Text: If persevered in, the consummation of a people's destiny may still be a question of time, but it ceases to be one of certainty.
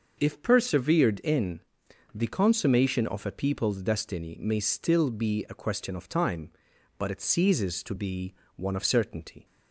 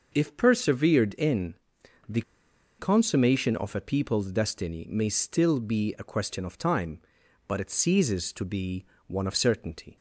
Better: first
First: pauses between "be" and "one"; slight; at 8.3 s; 0.22 s long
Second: pauses between "the" and "consummation"; noticeable; at 2.2 s; 0.57 s long // pauses between "be" and "one"; slight; at 8.8 s; 0.22 s long

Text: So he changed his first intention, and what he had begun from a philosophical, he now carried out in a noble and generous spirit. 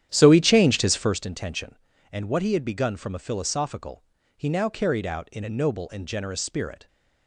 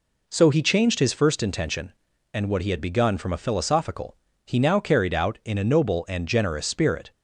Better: second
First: starts louder than the rest; strong; until 1.2 s; 10.5 dB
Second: none

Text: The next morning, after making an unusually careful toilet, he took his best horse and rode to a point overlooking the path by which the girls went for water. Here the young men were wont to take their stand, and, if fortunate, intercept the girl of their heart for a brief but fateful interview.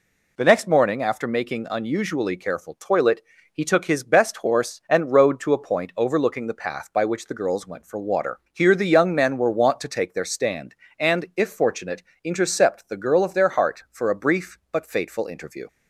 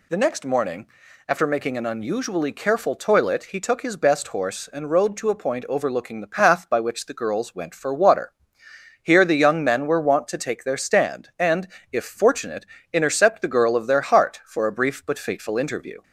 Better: second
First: skips "an"; at 1.6 s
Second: none

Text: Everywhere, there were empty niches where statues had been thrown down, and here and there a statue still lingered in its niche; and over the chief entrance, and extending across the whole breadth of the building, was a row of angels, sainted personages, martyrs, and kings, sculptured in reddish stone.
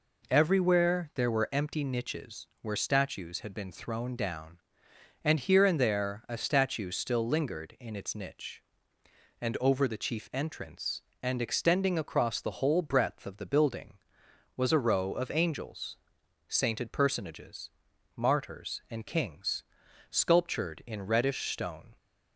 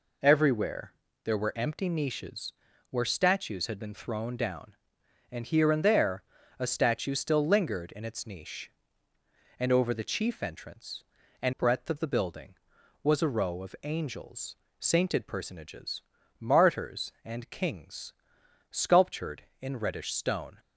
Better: first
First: none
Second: pauses between "niches" and "where"; slight; at 2.5 s; 0.36 s long // pauses between "there" and "a"; slight; at 6.2 s; 0.34 s long // skips "extending across the whole"; at 11.5 s

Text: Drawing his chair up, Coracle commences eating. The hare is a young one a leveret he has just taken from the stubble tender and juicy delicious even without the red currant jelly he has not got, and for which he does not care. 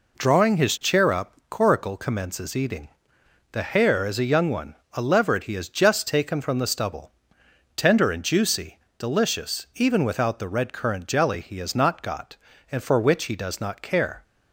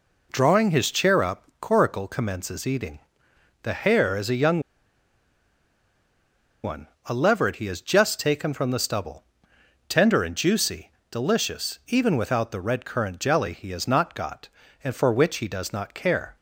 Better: first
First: pauses between "one" and "a"; slight; at 4.7 s; 0.18 s long // pauses between "stubble" and "tender"; noticeable; at 7.1 s; 0.64 s long // pauses between "juicy" and "delicious"; slight; at 8.7 s; 0.18 s long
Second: pauses between "young" and "one"; strong; at 4.5 s; 2.0 s long // pauses between "one" and "a"; slight; at 6.8 s; 0.18 s long // pauses between "stubble" and "tender"; noticeable; at 9.2 s; 0.64 s long // pauses between "juicy" and "delicious"; slight; at 10.9 s; 0.18 s long

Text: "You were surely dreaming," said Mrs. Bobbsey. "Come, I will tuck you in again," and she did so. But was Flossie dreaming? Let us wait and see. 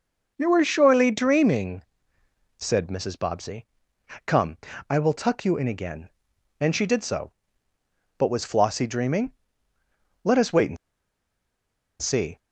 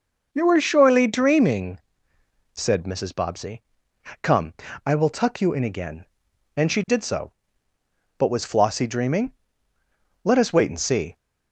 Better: second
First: pauses between "and" and "see"; strong; at 10.7 s; 1.2 s long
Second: none

